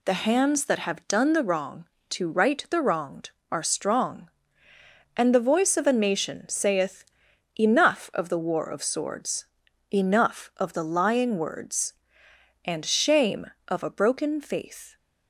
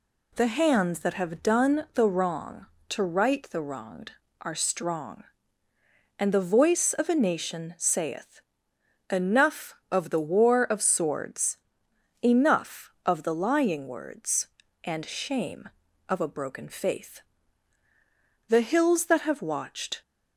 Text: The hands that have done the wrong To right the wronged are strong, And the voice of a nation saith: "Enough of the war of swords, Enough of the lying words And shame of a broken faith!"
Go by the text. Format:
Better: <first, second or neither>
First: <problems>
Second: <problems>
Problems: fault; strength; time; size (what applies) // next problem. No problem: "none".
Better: first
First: none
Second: goes on to say "The hills that have watched"; from 18.4 s on; 1.5 s long